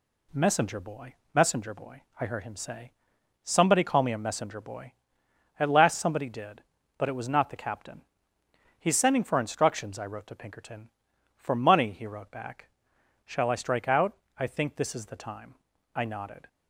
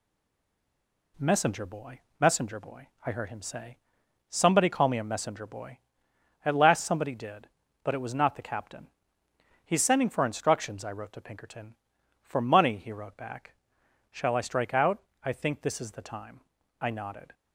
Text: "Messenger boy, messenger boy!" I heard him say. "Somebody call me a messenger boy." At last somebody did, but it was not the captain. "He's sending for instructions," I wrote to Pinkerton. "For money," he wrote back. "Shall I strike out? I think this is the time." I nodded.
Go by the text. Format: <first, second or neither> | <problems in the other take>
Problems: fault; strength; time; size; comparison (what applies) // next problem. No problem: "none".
first | stays silent before the first word; until 1.1 s; 1.1 s long